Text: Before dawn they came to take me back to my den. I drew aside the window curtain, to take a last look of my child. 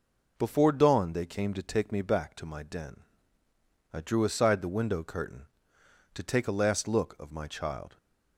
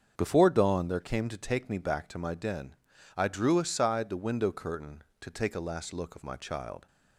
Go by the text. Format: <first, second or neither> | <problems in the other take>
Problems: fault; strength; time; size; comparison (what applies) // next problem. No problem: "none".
first | starts louder than the rest; strong; until 1.1 s; 7 dB // says "there" for "they"; at 0.8 s